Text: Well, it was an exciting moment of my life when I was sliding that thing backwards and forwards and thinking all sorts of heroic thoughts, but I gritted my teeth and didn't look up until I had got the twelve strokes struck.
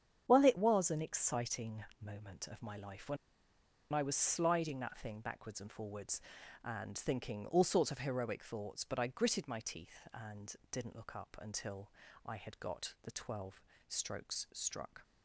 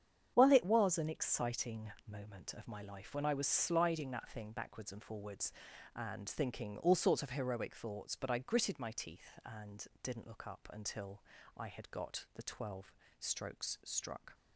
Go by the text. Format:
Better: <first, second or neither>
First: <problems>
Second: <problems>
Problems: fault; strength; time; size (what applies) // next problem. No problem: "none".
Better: second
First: starts louder than the rest; strong; until 1.2 s; 8 dB // pauses between "exciting" and "moment"; slight; at 1.8 s; 0.18 s long // pauses between "when" and "I"; noticeable; at 3.1 s; 0.75 s long // pauses between "and" and "didn't"; slight; at 10.5 s; 0.16 s long // pauses between "until" and "I"; slight; at 11.9 s; 0.34 s long // pauses between "twelve" and "strokes"; slight; at 13.6 s; 0.26 s long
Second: starts louder than the rest; strong; until 1.3 s; 8 dB // pauses between "exciting" and "moment"; slight; at 1.9 s; 0.16 s long // pauses between "and" and "didn't"; slight; at 9.8 s; 0.16 s long // pauses between "until" and "I"; slight; at 11.2 s; 0.34 s long // pauses between "twelve" and "strokes"; slight; at 12.9 s; 0.26 s long